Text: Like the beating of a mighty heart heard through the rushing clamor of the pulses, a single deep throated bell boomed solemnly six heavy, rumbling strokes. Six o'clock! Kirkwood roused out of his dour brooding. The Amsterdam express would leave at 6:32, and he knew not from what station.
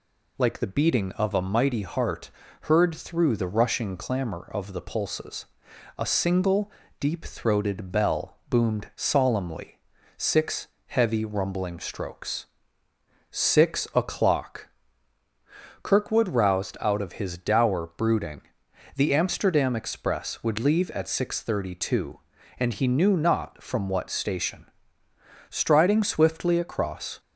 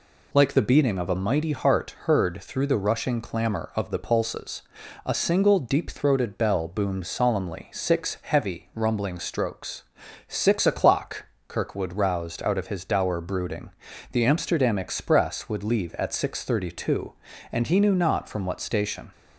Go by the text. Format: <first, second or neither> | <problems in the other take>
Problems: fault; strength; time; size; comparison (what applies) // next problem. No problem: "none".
second | pauses between "heart" and "heard"; slight; at 2.2 s; 0.32 s long // pauses between "single" and "deep"; slight; at 6.7 s; 0.26 s long // pauses between "solemnly" and "six"; at 9.7 s; 0.40 s long // pauses between "six" and "heavy"; slight; at 10.6 s; 0.20 s long // goes on to say "Striding swiftly across"; strong; from 25.5 s on; 1.6 s long